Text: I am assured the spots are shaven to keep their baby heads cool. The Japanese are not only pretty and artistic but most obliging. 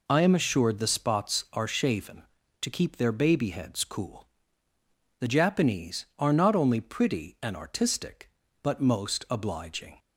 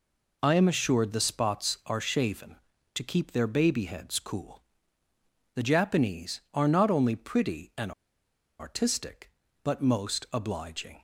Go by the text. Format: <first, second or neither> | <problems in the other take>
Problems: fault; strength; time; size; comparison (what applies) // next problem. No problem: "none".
first | pauses between "and" and "artistic"; noticeable; at 7.9 s; 0.68 s long